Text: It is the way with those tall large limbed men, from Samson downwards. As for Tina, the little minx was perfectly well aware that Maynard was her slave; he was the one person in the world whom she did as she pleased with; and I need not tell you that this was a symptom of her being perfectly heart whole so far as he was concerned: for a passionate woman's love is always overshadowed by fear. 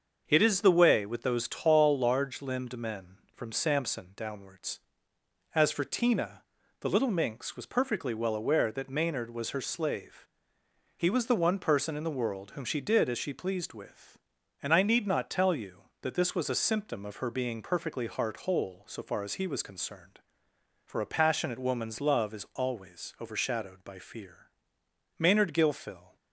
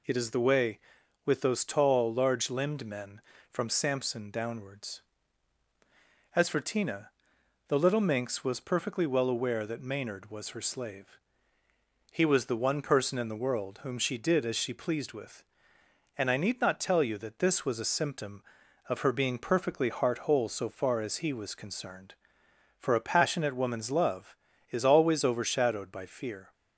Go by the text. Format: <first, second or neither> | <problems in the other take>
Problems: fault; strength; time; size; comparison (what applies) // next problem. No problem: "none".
second | starts louder than the rest; until 1.2 s; 6.5 dB // goes on to say "Maynard Gilfil"; noticeable; from 25.1 s on; 0.96 s long